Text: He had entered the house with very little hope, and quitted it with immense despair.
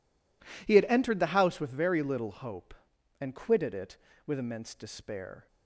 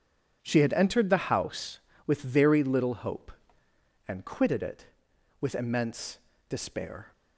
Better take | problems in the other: first | says "She" for "He"; at 0.4 s // pauses between "immense" and "despair"; slight; at 6.1 s; 0.30 s long

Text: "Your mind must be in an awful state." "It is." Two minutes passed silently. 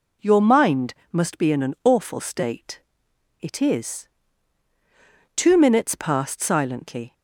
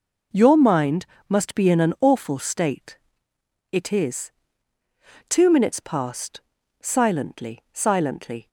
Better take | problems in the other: first | pauses between "mind" and "must"; slight; at 1.0 s; 0.24 s long; slight in the first // pauses between "passed" and "silently"; at 6.3 s; 0.40 s long // says "silently" twice; at 7.7 s

